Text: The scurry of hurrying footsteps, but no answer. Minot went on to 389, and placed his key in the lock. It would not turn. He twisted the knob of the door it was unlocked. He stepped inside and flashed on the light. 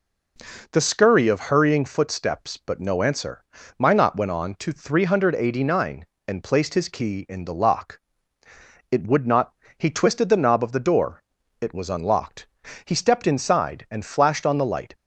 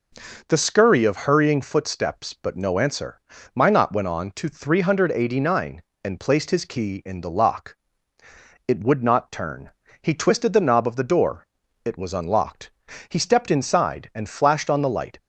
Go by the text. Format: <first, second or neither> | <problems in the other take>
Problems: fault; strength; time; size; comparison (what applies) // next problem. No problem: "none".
second | skips "turn"; at 9.6 s // pauses between "door" and "it"; at 11.2 s; 0.40 s long; also in the second